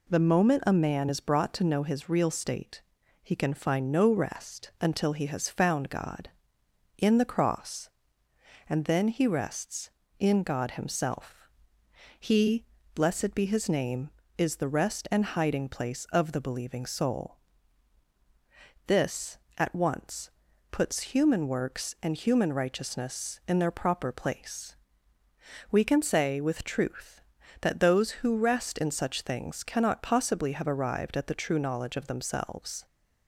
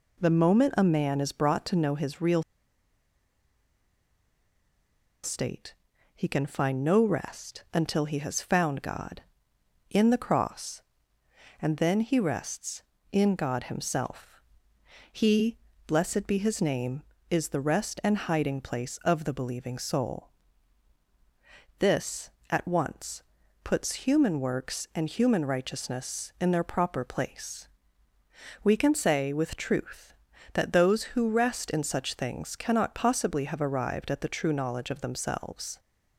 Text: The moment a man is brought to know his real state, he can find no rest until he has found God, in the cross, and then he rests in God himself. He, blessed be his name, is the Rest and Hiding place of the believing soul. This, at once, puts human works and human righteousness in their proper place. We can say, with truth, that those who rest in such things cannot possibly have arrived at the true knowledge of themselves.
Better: first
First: none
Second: pauses between "real" and "state"; strong; at 2.4 s; 2.8 s long

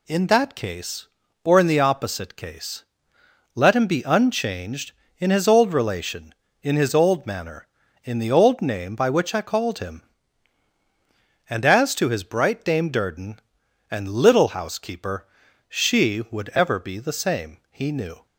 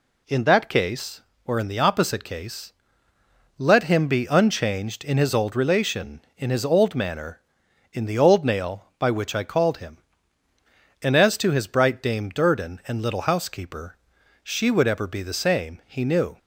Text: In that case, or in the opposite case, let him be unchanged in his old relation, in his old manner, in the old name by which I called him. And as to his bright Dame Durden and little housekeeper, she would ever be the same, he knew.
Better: first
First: none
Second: says "nail" for "name"; at 8.4 s

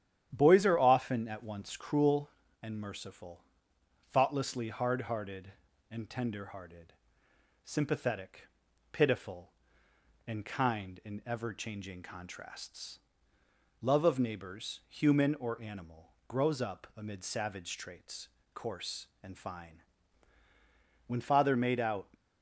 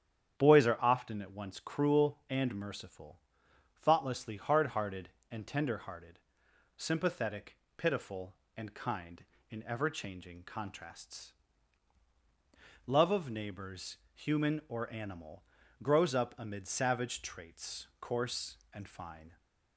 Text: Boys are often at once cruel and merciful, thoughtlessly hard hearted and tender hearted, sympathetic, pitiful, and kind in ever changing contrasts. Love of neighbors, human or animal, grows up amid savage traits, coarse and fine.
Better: second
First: starts louder than the rest; strong; until 1.3 s; 10.5 dB // goes on to say "When father made out"; noticeable; from 21.0 s on; 1.0 s long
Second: starts louder than the rest; strong; until 1.4 s; 9 dB

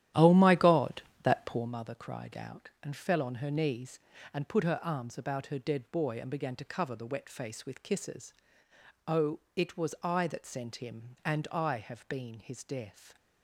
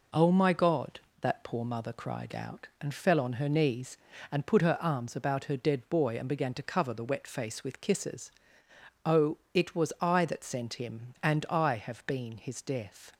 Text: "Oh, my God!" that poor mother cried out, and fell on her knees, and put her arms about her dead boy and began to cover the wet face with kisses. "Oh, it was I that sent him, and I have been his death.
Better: second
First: starts louder than the rest; strong; until 1.7 s; 12 dB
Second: none

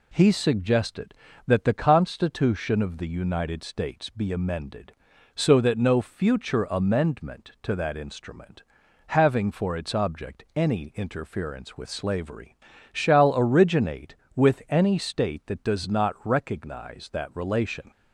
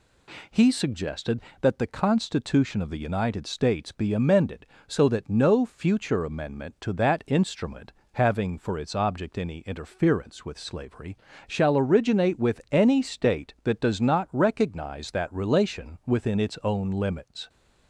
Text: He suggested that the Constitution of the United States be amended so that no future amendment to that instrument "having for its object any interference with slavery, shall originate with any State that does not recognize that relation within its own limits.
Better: second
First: pauses between "instrument" and "having"; at 8.6 s; 0.44 s long // stops before "within its own limits"; at 17.9 s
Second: pauses between "instrument" and "having"; slight; at 7.9 s; 0.18 s long

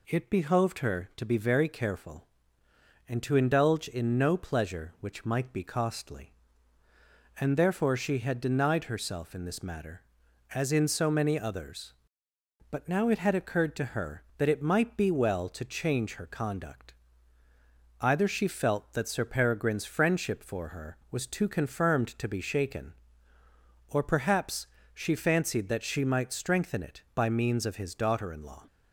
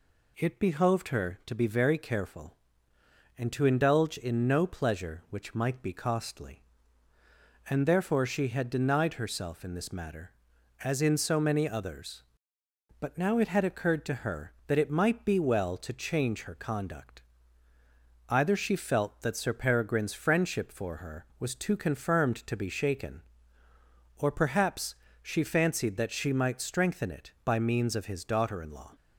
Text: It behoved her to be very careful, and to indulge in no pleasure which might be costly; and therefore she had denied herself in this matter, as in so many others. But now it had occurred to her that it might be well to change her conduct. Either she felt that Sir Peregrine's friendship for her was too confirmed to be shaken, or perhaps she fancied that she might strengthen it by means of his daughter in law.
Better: neither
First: pauses between "perhaps" and "she"; slight; at 24.6 s; 0.26 s long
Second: pauses between "perhaps" and "she"; slight; at 24.9 s; 0.26 s long

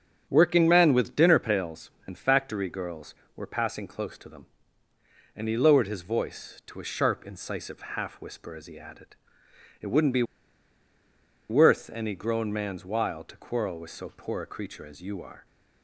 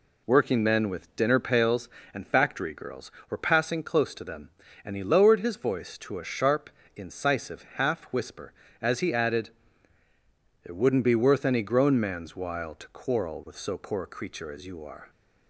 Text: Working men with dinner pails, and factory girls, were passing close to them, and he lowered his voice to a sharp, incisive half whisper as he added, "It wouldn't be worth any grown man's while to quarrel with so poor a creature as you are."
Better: second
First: starts louder than the rest; until 1.3 s; 6.5 dB // pauses between "incisive" and "half"; slight; at 7.7 s; 0.16 s long // pauses between "be" and "worth"; strong; at 10.2 s; 1.2 s long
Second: none

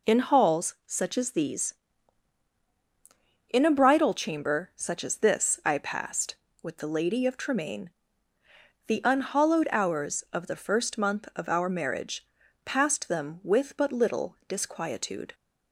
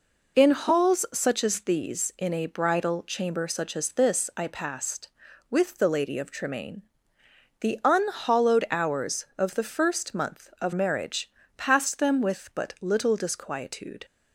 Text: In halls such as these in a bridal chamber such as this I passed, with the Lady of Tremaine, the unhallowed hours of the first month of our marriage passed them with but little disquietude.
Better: first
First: pauses between "marriage" and "passed"; at 12.2 s; 0.38 s long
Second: skips "our"; at 10.7 s // pauses between "marriage" and "passed"; slight; at 11.2 s; 0.28 s long

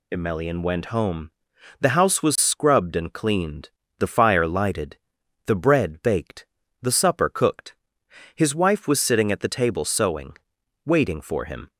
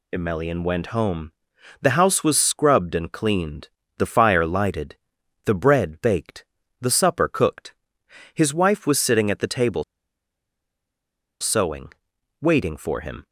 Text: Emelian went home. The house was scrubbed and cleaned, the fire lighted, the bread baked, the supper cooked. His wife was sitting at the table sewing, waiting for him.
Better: first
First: none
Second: pauses between "table" and "sewing"; strong; at 9.8 s; 1.5 s long

